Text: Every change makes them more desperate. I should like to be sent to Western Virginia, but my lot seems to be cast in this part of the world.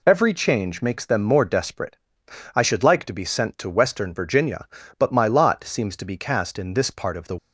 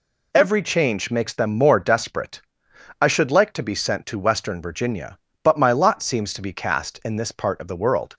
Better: second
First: stops before "world"; at 7.3 s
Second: none

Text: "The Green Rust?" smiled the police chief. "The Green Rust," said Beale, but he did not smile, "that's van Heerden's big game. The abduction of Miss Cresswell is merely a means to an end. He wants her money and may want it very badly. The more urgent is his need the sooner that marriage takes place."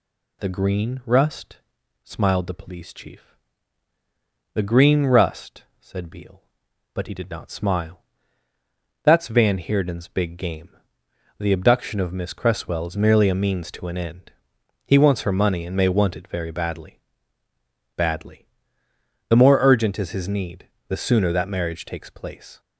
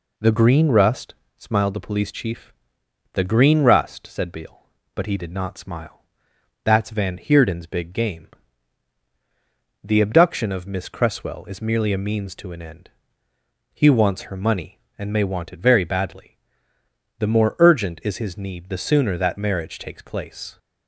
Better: second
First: says "badly" twice; at 17.9 s // pauses between "need" and "the"; slight; at 20.6 s; 0.20 s long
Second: none

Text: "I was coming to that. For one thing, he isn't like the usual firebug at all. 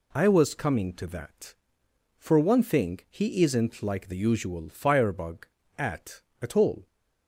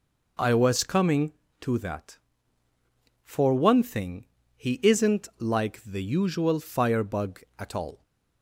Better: second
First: says "at" twice; at 6.4 s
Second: none

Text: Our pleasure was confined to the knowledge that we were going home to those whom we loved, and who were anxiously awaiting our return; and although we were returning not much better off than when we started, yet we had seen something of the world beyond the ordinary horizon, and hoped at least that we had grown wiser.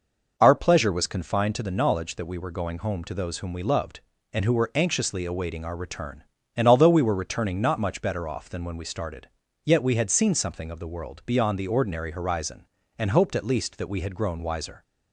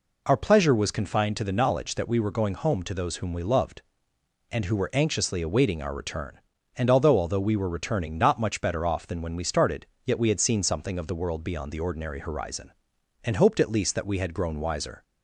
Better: first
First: none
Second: says "although" twice; at 7.1 s

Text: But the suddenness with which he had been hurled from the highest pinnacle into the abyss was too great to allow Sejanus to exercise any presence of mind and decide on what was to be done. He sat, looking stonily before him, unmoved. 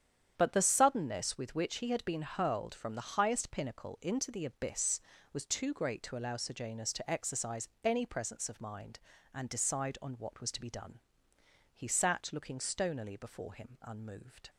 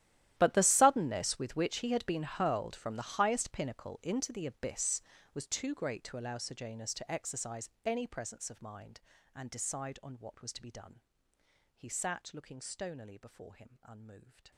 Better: first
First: starts louder than the rest; strong; until 1.3 s; 9 dB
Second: gets quieter; strong; throughout; 20 dB // starts louder than the rest; strong; until 1.3 s; 12.5 dB

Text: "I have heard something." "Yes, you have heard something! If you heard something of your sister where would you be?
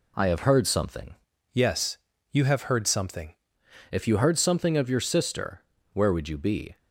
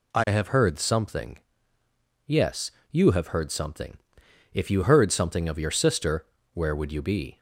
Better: second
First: changes voice from "Yes" to "something"; from 1.5 to 3.3 s; 1.8 s long // pauses between "sister" and "where"; slight; at 5.6 s; 0.28 s long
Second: pauses between "sister" and "where"; slight; at 6.2 s; 0.26 s long

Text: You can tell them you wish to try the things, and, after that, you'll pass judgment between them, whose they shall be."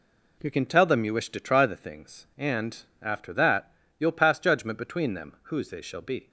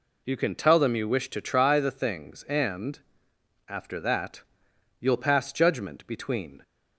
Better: first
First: none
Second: stops before "them whose they shall be"; at 6.6 s

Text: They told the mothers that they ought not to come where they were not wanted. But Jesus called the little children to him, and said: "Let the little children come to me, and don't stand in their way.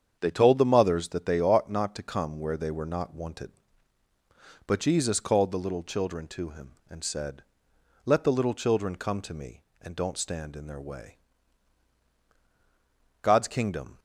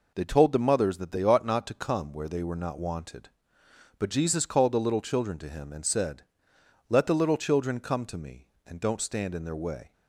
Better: second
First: starts louder than the rest; strong; until 1.2 s; 7.5 dB // goes on to say "God's Kingdom"; noticeable; from 13.2 s on; 0.76 s long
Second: none

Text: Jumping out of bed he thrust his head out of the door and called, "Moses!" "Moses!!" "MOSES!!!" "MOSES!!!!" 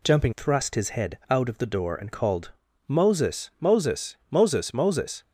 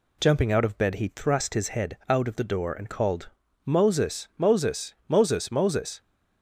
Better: second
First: skips "out of bed he"; at 0.3 s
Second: none

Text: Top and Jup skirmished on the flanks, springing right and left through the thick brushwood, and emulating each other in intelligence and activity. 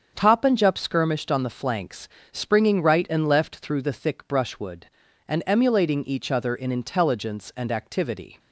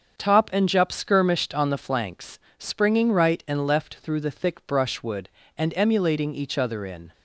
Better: first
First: starts louder than the rest; strong; until 1.1 s; 7 dB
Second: starts louder than the rest; until 1.2 s; 7 dB // stops before "intelligence and activity"; at 7.1 s

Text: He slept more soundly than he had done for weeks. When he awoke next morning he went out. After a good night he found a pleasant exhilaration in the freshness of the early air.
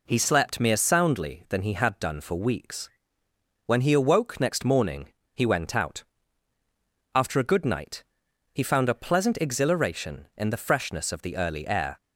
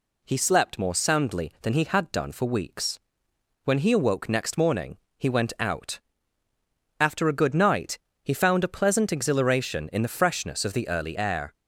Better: second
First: says "mere" for "more"; at 0.6 s // pauses between "morning" and "he"; slight; at 5.0 s; 0.26 s long // pauses between "night" and "he"; noticeable; at 8.0 s; 0.50 s long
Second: pauses between "morning" and "he"; slight; at 4.9 s; 0.20 s long // pauses between "night" and "he"; slight; at 7.9 s; 0.26 s long

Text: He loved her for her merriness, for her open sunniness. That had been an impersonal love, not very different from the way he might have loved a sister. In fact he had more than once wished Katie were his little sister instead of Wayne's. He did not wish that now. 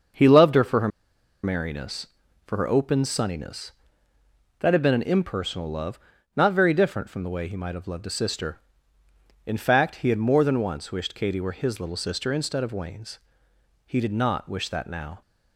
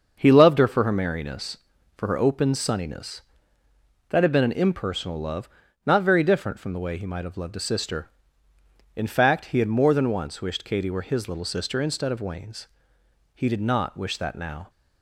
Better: second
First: starts louder than the rest; until 1.7 s; 6.5 dB // pauses between "her" and "merriness"; noticeable; at 0.8 s; 0.55 s long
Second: starts louder than the rest; until 1.2 s; 6.5 dB

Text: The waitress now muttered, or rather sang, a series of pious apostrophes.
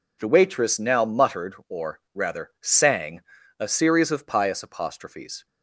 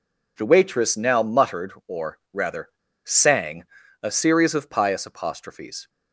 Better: first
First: none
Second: pauses between "rather" and "sang"; slight; at 2.6 s; 0.34 s long

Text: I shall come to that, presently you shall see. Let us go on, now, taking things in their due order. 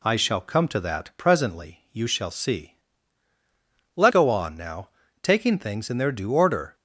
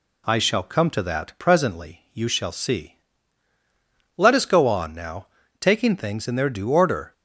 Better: second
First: skips "us"; at 4.1 s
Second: none

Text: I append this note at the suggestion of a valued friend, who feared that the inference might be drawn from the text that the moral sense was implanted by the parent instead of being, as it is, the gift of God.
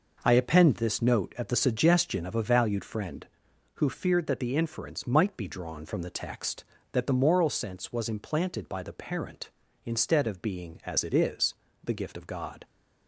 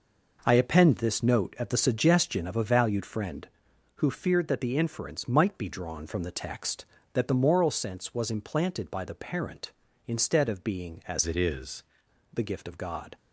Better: first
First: none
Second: changes voice from "it" to "is"; from 11.2 to 11.8 s; 0.6 s long

